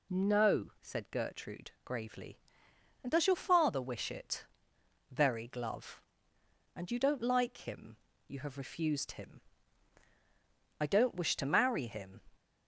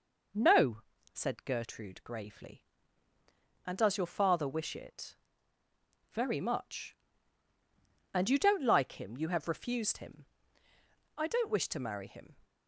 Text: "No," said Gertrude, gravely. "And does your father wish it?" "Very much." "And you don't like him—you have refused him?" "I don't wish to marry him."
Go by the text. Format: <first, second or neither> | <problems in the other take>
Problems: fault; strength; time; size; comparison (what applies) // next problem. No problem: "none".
second | says "glove" for "much"; at 5.4 s